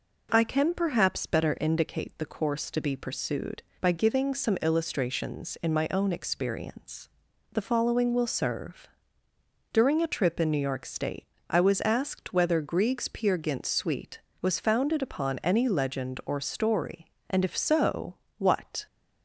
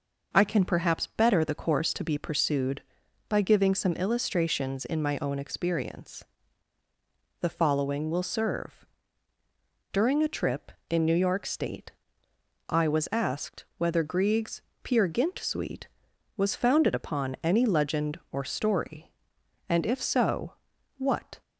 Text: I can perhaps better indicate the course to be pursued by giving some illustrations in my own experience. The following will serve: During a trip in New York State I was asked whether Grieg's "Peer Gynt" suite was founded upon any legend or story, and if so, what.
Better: first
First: pauses between "State" and "I"; slight; at 11.2 s; 0.24 s long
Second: skips "indicate"; at 1.4 s // pauses between "State" and "I"; noticeable; at 11.9 s; 0.78 s long // pauses between "Grieg's" and "Peer"; slight; at 14.6 s; 0.22 s long

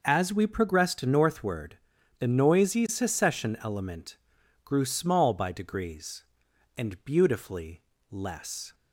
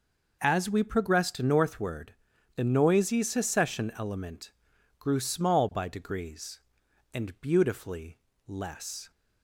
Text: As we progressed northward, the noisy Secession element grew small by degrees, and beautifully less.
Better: neither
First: pauses between "element" and "grew"; noticeable; at 4.1 s; 0.48 s long // pauses between "beautifully" and "less"; slight; at 7.8 s; 0.28 s long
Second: pauses between "element" and "grew"; noticeable; at 4.5 s; 0.48 s long // pauses between "beautifully" and "less"; slight; at 8.1 s; 0.28 s long

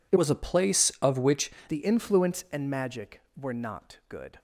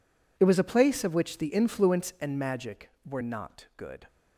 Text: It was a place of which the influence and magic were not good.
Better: second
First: changes voice from "was" to "which"; from 0.1 to 1.5 s; 1.4 s long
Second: none

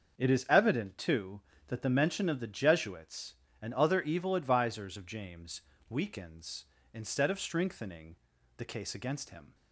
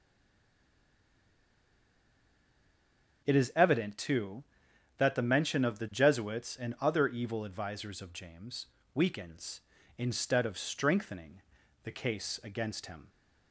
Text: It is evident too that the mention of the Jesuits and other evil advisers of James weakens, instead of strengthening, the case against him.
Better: first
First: starts louder than the rest; until 1.2 s; 6.5 dB // pauses between "James" and "weakens"; slight; at 5.6 s; 0.28 s long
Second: stays silent before the first word; strong; until 3.2 s; 3.2 s long // starts louder than the rest; until 4.2 s; 6.5 dB // pauses between "James" and "weakens"; slight; at 8.6 s; 0.26 s long

